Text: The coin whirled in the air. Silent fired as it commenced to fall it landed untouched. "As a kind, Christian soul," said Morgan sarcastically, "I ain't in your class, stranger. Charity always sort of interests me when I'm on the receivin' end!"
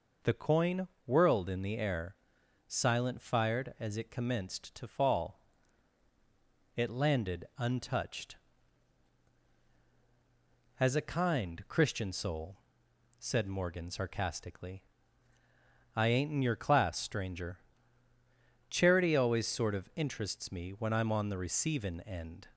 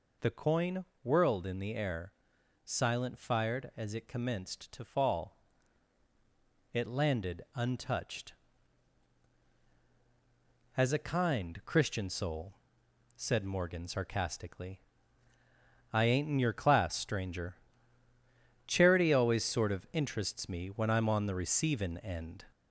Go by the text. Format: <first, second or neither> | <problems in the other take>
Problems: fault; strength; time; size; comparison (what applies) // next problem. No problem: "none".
first | gets louder; slight; throughout; 3.5 dB // pauses between "coin" and "whirled"; slight; at 0.8 s; 0.20 s long; slight in the first // pauses between "fall" and "it"; strong; at 5.3 s; 1.3 s long; strong in the first